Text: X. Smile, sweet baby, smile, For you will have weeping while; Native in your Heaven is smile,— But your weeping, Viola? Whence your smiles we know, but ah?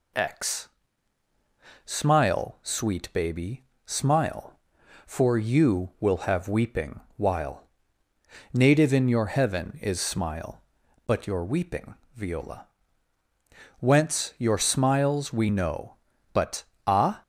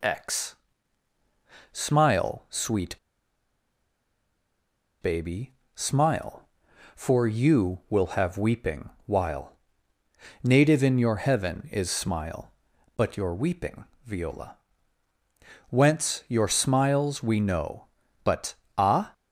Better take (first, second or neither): first